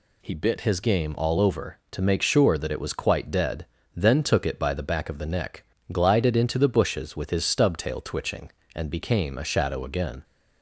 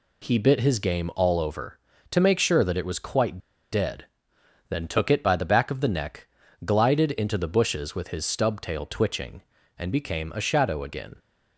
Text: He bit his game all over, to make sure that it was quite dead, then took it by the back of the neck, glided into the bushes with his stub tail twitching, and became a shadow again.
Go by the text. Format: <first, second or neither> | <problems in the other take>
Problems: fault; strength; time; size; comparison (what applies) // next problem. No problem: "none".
first | pauses between "quite" and "dead"; slight; at 3.3 s; 0.33 s long